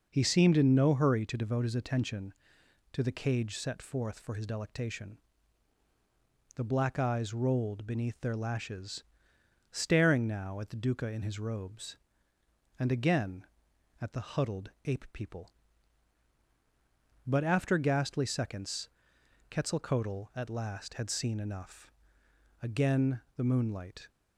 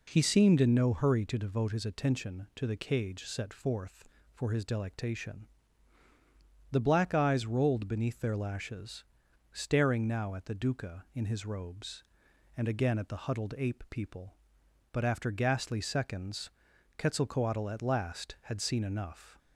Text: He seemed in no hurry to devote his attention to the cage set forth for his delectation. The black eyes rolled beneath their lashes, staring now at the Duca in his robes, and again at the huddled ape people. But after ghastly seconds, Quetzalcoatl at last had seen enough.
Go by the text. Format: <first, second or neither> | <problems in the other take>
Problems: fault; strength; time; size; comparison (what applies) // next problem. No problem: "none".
second | pauses between "huddled" and "ape"; slight; at 14.7 s; 0.16 s long // goes on to say "Again the moonlight"; from 22.6 s on; 1.4 s long